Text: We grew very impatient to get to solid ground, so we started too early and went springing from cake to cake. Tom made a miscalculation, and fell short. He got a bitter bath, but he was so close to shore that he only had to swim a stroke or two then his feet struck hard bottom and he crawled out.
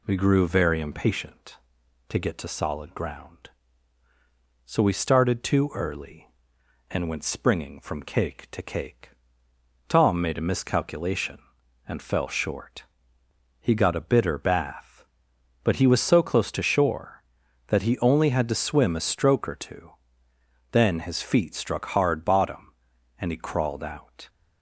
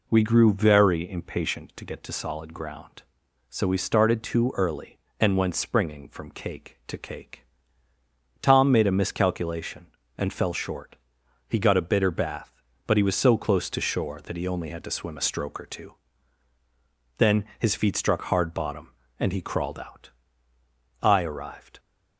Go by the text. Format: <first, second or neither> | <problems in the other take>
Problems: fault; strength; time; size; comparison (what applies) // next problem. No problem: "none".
first | pauses between "two" and "then"; strong; at 15.9 s; 1.2 s long; noticeable in the first // goes on to say "I arrived"; noticeable; from 21.0 s on; 0.78 s long